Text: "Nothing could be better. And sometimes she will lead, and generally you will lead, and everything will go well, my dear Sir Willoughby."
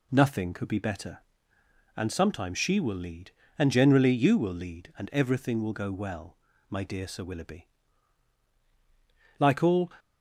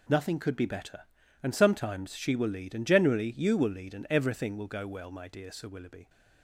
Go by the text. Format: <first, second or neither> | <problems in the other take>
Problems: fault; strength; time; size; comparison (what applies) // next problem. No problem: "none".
second | goes on to say "Like all"; from 9.3 s on; 0.54 s long